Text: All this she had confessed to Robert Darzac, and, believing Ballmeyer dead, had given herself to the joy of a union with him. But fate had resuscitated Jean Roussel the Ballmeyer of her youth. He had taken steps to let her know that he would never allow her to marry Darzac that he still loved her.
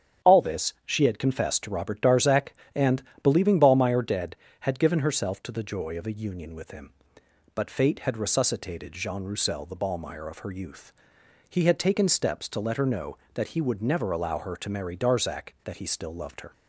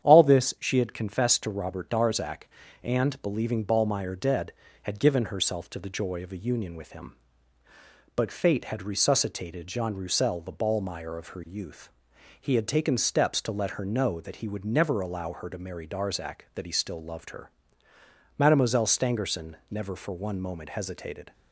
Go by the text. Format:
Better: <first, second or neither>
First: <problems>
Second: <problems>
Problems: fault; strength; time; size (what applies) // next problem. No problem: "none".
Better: first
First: starts louder than the rest; strong; until 1.3 s; 9 dB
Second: starts louder than the rest; strong; until 1.1 s; 9 dB // goes on to say "Mademoiselle Stangerson never for one moment hesitated"; strong; from 18.3 s on; 2.9 s long